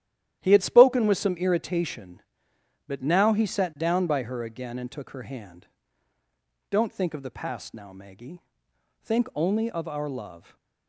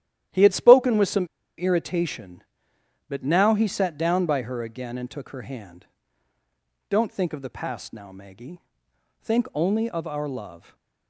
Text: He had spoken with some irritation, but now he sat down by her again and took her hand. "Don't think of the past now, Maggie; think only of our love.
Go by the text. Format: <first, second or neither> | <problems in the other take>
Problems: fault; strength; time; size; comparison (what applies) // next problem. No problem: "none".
first | starts louder than the rest; strong; until 1.6 s; 11.5 dB; strong in the first // pauses between "some" and "irritation"; slight; at 1.2 s; 0.31 s long // stays silent after the last word; slight; from 10.5 s on; 0.5 s long